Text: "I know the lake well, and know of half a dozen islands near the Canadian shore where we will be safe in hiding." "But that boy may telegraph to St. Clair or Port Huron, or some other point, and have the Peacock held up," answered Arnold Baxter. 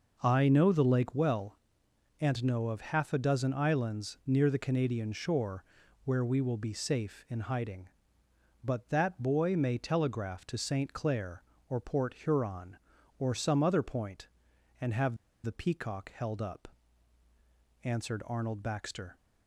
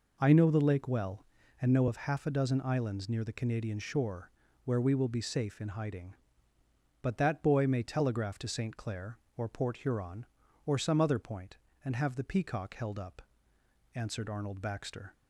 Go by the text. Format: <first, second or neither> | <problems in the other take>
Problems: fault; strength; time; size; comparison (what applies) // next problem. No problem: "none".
second | pauses between "shore" and "where"; at 5.6 s; 0.42 s long; slight in the second // pauses between "have" and "the"; slight; at 15.1 s; 0.27 s long